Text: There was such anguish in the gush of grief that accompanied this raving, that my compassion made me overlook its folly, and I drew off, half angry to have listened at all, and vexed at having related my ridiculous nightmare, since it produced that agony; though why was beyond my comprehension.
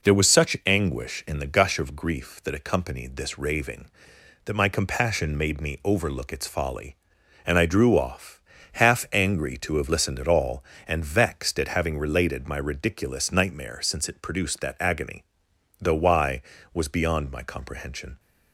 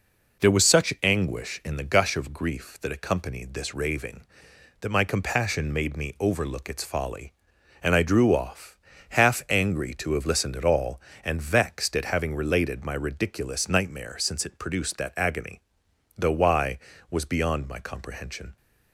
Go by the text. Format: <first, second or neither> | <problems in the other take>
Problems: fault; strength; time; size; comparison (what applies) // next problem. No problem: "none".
neither | none